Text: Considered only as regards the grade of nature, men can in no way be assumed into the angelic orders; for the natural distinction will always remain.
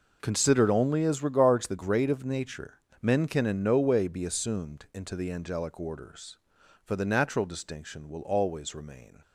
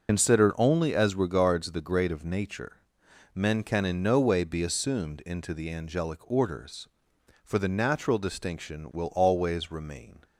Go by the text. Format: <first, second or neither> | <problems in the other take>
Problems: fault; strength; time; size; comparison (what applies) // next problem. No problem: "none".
first | loses the start of "Considered"; at 0.0 s; 70 ms